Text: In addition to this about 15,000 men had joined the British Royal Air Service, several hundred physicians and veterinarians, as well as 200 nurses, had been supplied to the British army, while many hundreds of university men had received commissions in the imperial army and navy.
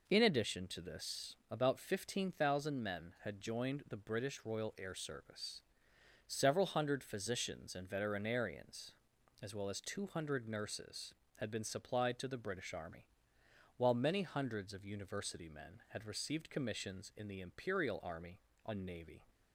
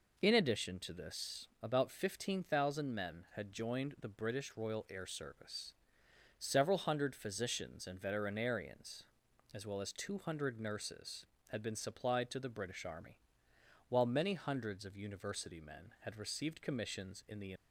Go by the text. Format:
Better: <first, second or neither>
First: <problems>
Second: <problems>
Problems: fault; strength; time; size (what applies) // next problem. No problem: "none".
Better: first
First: none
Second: stops before "imperial army and navy"; at 17.5 s